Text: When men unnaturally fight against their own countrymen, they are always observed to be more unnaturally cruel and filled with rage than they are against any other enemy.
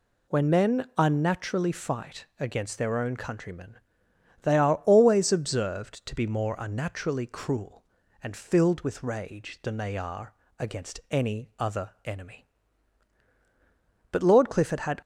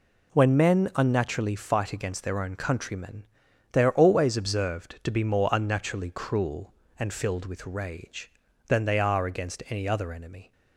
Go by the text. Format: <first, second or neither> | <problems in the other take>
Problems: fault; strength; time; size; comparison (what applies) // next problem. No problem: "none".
second | pauses between "are" and "against"; slight; at 10.3 s; 0.24 s long // goes on to say "But Lord Clifford had"; noticeable; from 14.1 s on; 0.90 s long